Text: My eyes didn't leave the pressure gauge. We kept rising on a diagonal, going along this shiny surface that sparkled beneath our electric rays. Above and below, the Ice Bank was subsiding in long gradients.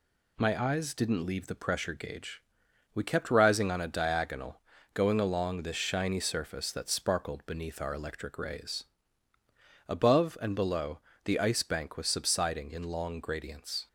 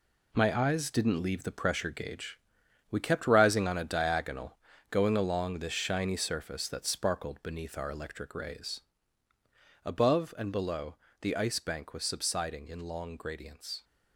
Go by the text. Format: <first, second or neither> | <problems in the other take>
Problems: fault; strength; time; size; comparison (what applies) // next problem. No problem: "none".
first | gets quieter; strong; throughout; 8.5 dB